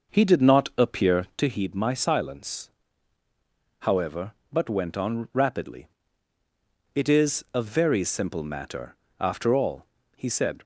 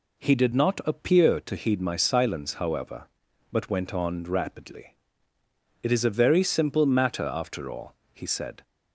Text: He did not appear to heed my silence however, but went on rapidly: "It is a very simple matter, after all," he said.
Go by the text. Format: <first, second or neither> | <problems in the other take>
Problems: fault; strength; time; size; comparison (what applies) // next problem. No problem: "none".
second | starts louder than the rest; noticeable; until 1.6 s; 6 dB // pauses between "silence" and "however"; at 2.6 s; 1.1 s long